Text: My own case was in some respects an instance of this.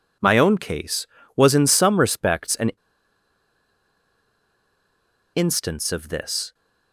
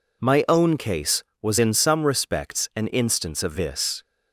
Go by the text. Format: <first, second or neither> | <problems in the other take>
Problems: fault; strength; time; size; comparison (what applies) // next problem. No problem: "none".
second | pauses between "an" and "instance"; strong; at 2.7 s; 2.6 s long